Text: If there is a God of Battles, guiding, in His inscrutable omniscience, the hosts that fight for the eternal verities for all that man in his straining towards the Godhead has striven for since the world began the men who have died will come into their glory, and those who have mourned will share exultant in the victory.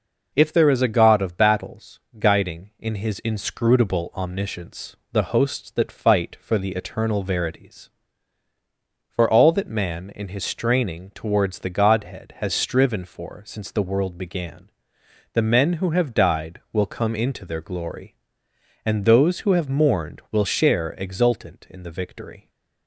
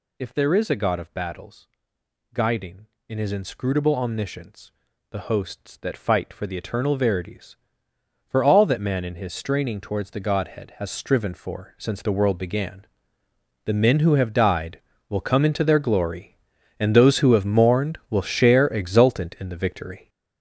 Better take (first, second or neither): first